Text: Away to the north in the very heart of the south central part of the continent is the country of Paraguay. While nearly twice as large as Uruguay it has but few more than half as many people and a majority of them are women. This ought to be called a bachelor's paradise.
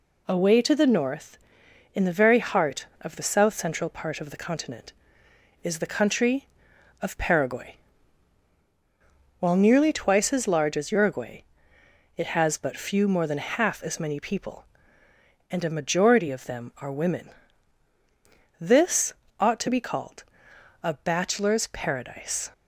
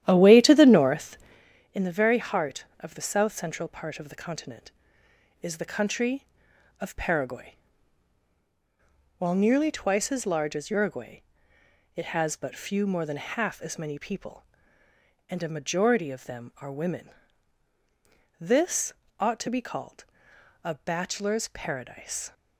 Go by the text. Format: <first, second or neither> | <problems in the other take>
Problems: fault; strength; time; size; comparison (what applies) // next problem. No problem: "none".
first | starts louder than the rest; strong; until 1.5 s; 11.5 dB // pauses between "Uruguay" and "it"; noticeable; at 11.2 s; 0.72 s long; noticeable in the first // pauses between "This" and "ought"; slight; at 18.9 s; 0.28 s long; slight in the first // pauses between "called" and "a"; noticeable; at 20.0 s; 0.60 s long; noticeable in the first